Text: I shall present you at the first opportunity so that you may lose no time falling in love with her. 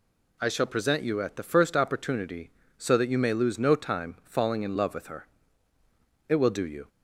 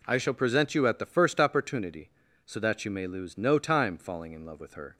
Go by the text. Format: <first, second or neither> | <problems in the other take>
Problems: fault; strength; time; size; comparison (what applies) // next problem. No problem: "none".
second | goes on to say "It will do you"; noticeable; from 6.2 s on; 0.62 s long